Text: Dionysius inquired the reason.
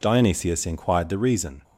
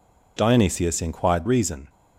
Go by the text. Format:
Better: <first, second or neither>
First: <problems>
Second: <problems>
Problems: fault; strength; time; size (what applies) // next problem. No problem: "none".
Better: first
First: none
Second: skips "the"; at 1.4 s